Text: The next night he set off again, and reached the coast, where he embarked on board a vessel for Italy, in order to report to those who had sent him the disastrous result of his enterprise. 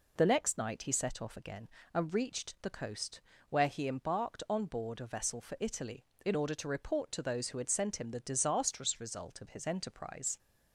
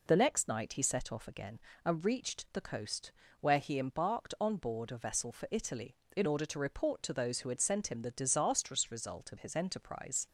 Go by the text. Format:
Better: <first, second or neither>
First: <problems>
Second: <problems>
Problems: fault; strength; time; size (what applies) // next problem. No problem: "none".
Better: neither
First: none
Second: none